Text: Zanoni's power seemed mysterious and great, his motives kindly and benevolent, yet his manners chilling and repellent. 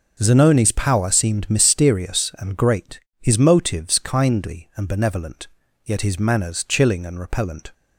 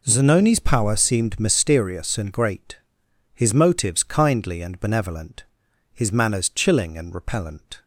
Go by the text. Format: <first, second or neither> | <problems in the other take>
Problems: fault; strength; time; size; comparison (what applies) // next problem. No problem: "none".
first | skips "yet"; at 5.6 s